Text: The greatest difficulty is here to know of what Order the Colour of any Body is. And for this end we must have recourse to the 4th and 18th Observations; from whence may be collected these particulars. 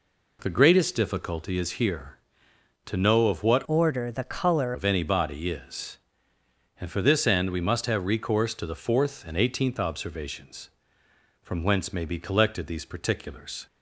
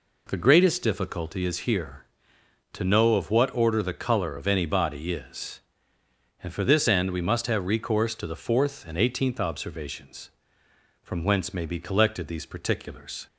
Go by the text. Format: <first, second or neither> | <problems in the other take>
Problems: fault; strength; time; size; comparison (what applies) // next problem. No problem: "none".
second | changes voice from "Order" to "Colour"; from 3.6 to 4.7 s; 1.1 s long